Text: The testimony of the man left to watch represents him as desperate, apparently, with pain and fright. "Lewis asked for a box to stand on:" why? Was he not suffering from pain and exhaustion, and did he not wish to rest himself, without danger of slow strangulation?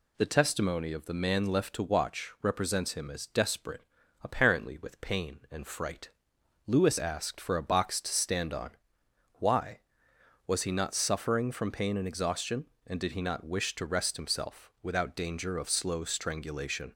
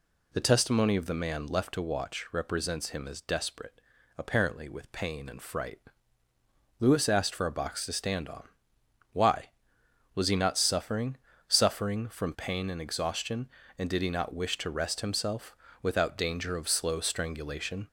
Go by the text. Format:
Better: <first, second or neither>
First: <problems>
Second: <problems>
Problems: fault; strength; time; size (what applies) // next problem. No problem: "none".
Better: first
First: none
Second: says "suffering" twice; at 11.4 s